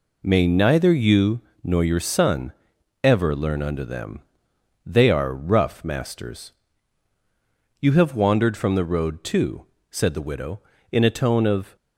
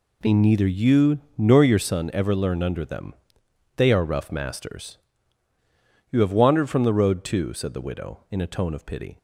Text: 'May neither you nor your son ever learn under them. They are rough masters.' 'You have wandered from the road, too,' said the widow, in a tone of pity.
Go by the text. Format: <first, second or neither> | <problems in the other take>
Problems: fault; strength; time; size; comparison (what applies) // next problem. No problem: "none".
second | pauses between "you" and "nor"; slight; at 1.4 s; 0.22 s long; slight in the second // pauses between "son" and "ever"; noticeable; at 2.5 s; 0.50 s long // stops before "pity"; at 11.7 s